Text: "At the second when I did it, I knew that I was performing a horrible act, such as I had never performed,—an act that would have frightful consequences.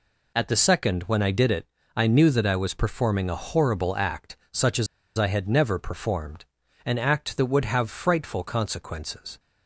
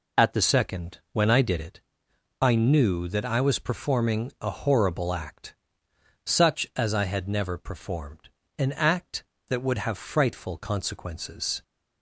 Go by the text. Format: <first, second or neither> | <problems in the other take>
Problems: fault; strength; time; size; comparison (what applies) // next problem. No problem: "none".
second | pauses between "as" and "I"; slight; at 4.8 s; 0.30 s long